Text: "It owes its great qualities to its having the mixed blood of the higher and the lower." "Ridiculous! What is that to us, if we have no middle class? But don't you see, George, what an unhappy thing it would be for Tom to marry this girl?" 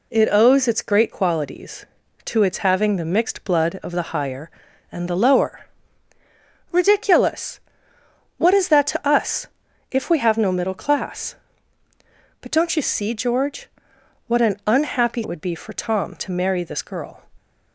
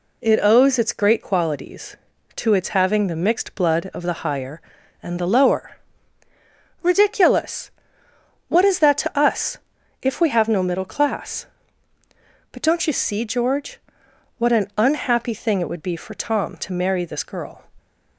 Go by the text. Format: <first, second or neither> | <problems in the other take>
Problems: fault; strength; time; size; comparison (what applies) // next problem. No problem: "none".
second | skips "thing"; at 15.2 s